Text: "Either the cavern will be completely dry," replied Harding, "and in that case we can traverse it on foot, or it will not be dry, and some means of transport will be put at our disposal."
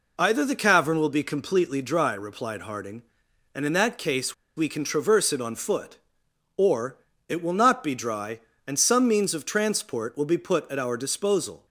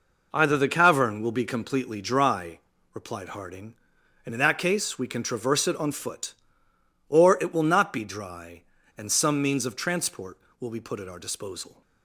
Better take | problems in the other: second | pauses between "case" and "we"; slight; at 4.3 s; 0.22 s long // pauses between "or" and "it"; slight; at 6.9 s; 0.32 s long

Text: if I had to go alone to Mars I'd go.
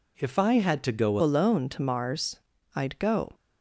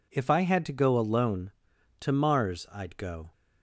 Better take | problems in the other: second | changes voice at "alone"; from 1.2 s on; 2.1 s long // pauses between "Mars" and "I'd"; at 2.3 s; 0.38 s long

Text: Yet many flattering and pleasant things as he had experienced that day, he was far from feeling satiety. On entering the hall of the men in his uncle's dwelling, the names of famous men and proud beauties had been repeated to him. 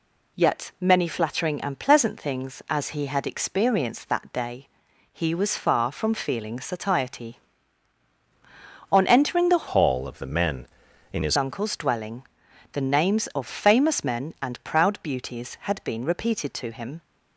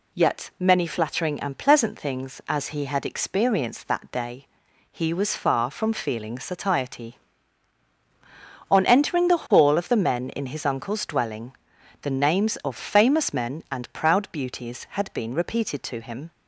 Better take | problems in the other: second | changes voice from "hall" to "his"; from 9.6 to 11.3 s; 1.7 s long

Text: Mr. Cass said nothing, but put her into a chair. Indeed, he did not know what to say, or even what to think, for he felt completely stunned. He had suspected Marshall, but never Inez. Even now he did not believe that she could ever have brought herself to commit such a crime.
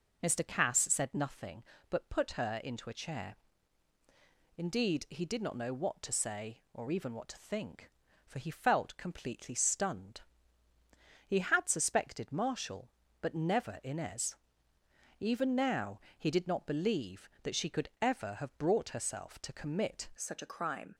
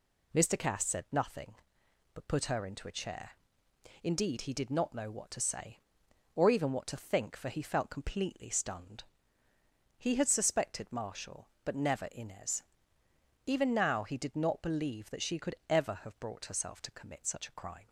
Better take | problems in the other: second | pauses between "now" and "he"; slight; at 15.9 s; 0.18 s long // changes voice at "such"; from 20.1 s on; 0.8 s long

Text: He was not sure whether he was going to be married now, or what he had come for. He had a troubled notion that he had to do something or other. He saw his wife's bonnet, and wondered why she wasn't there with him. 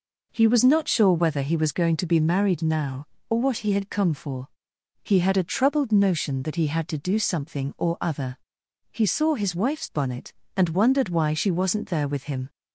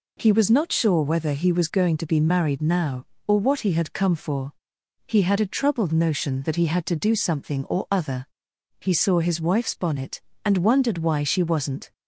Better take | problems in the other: first | stops before "there with him"; at 11.9 s

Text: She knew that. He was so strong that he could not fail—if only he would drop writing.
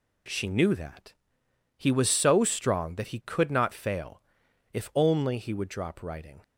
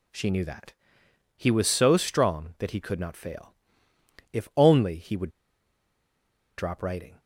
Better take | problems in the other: first | pauses between "would" and "drop"; strong; at 5.2 s; 1.2 s long

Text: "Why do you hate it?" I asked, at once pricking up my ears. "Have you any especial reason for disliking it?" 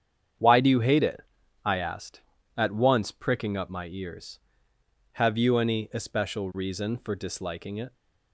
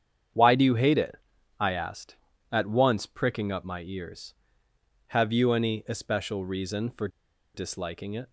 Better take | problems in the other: first | starts louder than the rest; strong; until 1.7 s; 8.5 dB; strong in the first // pauses between "for" and "disliking"; noticeable; at 7.0 s; 0.46 s long

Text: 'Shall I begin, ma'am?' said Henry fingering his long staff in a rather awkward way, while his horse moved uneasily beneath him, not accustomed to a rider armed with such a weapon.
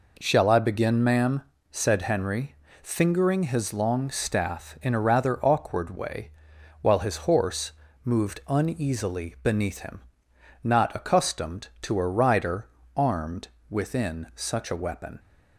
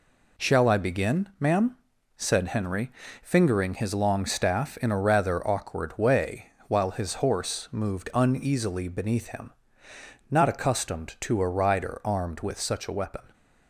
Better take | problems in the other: second | pauses between "Henry" and "fingering"; slight; at 2.5 s; 0.26 s long; slight in the second // pauses between "horse" and "moved"; slight; at 7.7 s; 0.32 s long // pauses between "rider" and "armed"; slight; at 12.6 s; 0.30 s long // says "within" for "with"; at 13.6 s

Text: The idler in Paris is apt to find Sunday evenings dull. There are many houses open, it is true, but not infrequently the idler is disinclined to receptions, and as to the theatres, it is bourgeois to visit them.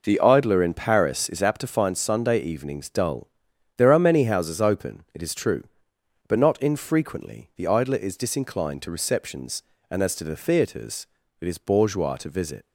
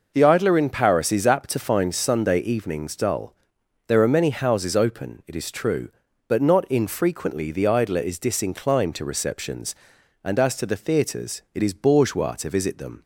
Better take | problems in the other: second | stops before "them"; at 12.6 s

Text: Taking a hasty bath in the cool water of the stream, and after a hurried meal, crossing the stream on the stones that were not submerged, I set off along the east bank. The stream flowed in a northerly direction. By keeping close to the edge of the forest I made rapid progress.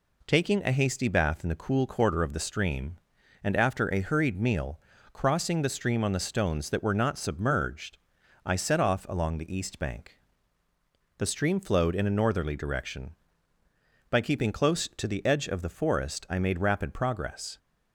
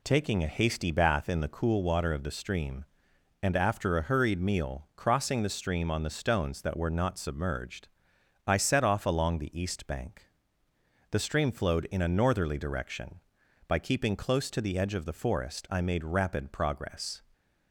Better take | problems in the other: second | says "quarter" for "water"; at 1.8 s

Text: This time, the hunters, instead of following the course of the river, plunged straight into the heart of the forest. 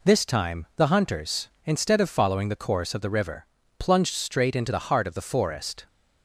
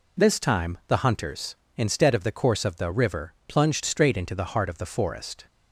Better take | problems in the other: first | skips "following"; at 2.2 s

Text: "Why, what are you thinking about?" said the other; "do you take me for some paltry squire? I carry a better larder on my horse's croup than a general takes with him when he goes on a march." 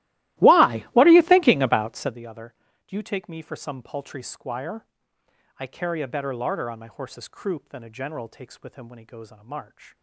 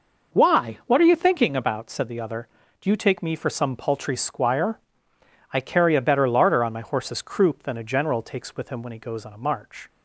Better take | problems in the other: second | starts louder than the rest; strong; until 2.3 s; 16.5 dB

